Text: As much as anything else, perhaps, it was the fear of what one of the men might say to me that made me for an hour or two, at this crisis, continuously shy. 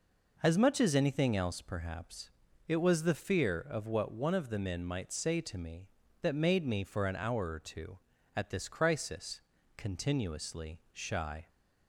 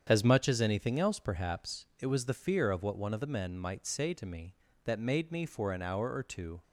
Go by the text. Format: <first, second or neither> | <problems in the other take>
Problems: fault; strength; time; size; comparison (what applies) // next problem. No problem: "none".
first | starts louder than the rest; strong; until 1.1 s; 8 dB // stops before "at this crisis continuously shy"; at 6.6 s